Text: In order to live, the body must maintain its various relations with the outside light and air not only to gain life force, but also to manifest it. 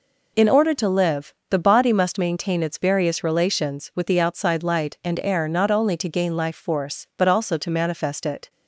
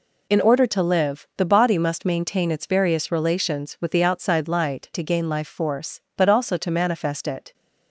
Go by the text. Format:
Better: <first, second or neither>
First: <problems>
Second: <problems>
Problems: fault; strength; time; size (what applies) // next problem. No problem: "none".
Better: first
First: none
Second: skips "and air not only"; at 4.9 s